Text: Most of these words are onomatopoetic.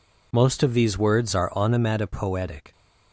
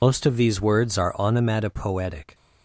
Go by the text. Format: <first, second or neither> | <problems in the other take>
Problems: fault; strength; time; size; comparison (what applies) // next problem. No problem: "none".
first | loses the start of "Most"; at 0.0 s; 65 ms